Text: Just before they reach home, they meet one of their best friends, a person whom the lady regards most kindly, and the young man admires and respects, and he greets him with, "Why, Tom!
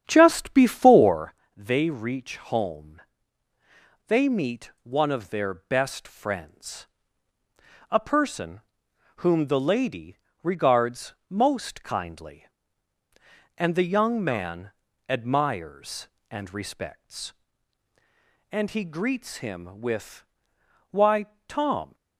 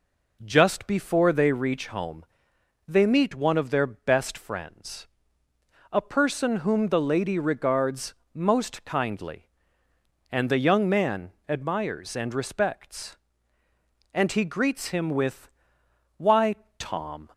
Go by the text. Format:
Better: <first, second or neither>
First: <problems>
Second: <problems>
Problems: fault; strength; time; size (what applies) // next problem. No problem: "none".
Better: second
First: starts louder than the rest; strong; until 1.4 s; 9 dB // pauses between "before" and "they"; slight; at 1.3 s; 0.24 s long // pauses between "person" and "whom"; noticeable; at 8.6 s; 0.56 s long // pauses between "lady" and "regards"; slight; at 10.1 s; 0.26 s long // pauses between "regards" and "most"; slight; at 11.1 s; 0.16 s long // pauses between "man" and "admires"; slight; at 14.7 s; 0.36 s long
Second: pauses between "regards" and "most"; slight; at 8.1 s; 0.18 s long // pauses between "man" and "admires"; slight; at 11.3 s; 0.16 s long